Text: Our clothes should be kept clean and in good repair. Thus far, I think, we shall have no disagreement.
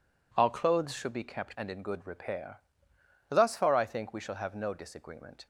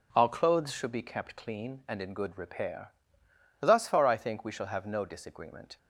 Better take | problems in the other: second | skips "clean"; at 1.5 s

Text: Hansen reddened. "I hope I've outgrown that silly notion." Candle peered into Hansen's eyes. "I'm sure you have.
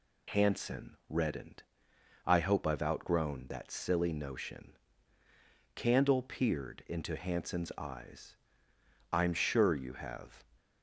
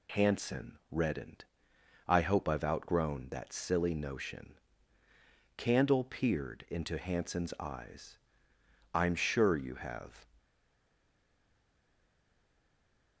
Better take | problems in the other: first | stays silent after the last word; strong; from 10.3 s on; 2.9 s long

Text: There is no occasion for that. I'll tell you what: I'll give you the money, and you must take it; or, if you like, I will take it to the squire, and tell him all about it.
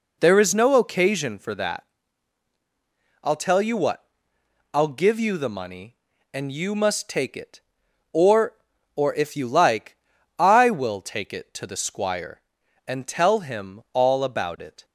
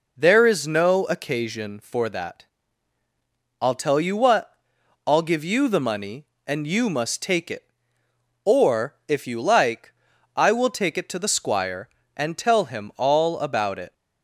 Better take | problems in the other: second | says "or" twice; at 8.9 s

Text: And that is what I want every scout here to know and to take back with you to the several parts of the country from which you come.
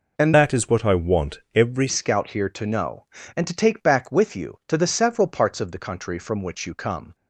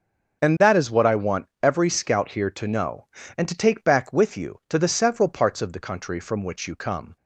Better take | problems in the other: second | changes voice from "that" to "every"; from 0.3 to 1.8 s; 1.5 s long // pauses between "want" and "every"; slight; at 1.3 s; 0.16 s long; slight in the second

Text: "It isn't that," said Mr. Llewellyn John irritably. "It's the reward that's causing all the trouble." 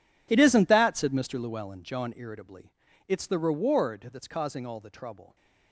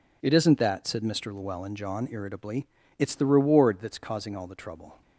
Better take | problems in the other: second | gets quieter; strong; throughout; 16.5 dB

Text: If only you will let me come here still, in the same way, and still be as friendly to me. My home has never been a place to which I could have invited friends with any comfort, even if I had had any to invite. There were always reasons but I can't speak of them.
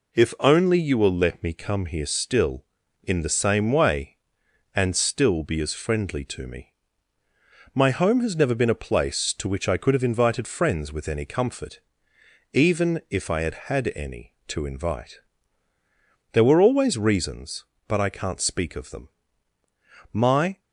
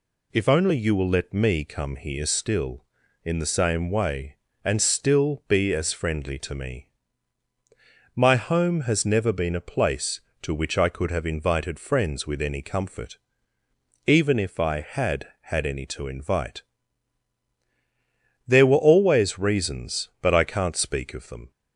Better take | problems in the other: second | goes on to say "My"; slight; from 20.1 s on; 0.48 s long

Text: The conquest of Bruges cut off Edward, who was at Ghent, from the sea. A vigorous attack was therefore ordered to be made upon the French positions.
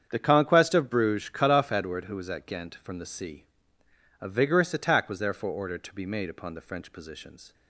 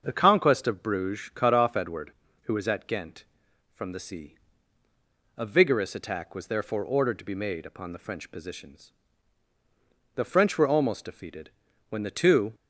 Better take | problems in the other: first | starts louder than the rest; until 1.0 s; 6.5 dB; strong in the first // goes on to say "The French were almost defeated when the two"; strong; from 10.1 s on; 2.3 s long

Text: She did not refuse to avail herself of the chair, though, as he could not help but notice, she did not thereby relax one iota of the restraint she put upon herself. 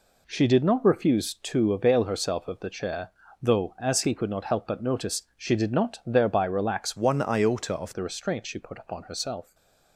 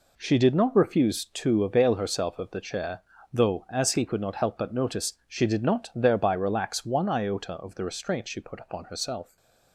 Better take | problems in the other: second | changes voice from "one" to "of"; from 6.9 to 7.9 s; 1.0 s long // stays silent after the last word; slight; from 9.4 s on; 0.5 s long; slight in the second

